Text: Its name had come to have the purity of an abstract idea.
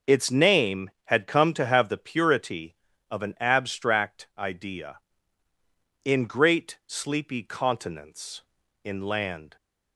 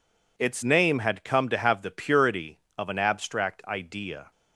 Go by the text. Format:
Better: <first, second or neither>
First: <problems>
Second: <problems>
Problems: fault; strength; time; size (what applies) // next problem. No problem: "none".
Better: second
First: starts louder than the rest; noticeable; until 1.2 s; 6 dB // goes on to say "In great sleepy continents in land"; strong; from 6.0 s on; 3.5 s long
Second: none